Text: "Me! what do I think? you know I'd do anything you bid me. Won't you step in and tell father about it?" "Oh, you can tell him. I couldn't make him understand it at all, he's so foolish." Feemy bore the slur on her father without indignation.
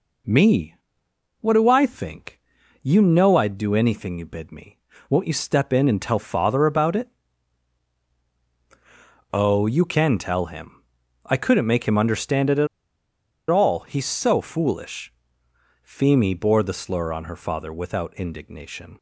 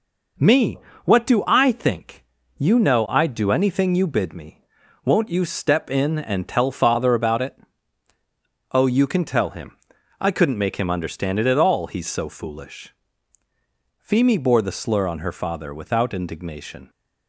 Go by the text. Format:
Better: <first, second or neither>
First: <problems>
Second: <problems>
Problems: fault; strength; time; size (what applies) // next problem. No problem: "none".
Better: second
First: pauses between "at" and "all"; noticeable; at 12.6 s; 0.83 s long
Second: none